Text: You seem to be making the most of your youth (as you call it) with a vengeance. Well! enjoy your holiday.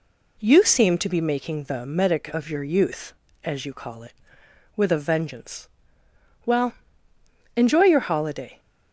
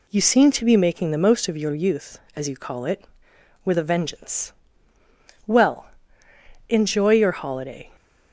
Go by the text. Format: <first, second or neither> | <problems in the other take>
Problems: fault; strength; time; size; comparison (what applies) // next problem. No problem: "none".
second | says "medic" for "most"; at 1.8 s